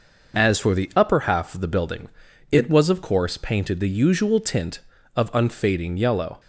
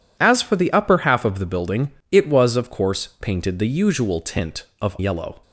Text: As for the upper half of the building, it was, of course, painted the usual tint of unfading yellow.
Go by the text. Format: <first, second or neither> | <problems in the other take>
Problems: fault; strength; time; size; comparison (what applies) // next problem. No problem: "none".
first | skips "unfading"; at 4.9 s